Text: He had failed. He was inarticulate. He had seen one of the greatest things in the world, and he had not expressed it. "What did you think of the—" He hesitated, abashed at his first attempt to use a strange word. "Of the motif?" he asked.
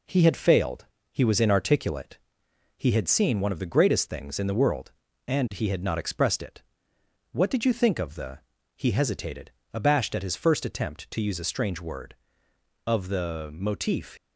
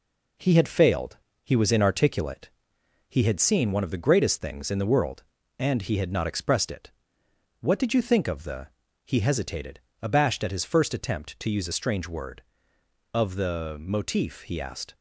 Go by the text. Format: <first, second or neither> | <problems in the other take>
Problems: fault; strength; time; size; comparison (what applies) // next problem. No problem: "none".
second | stops before "he asked"; at 14.1 s